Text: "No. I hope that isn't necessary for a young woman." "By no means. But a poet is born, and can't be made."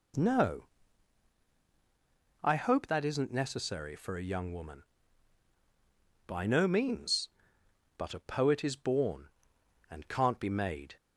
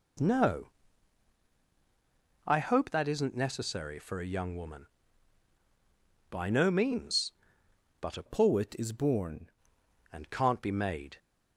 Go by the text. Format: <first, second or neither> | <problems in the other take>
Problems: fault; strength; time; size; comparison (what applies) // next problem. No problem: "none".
first | changes voice from "poet" to "born"; from 8.2 to 9.5 s; 1.3 s long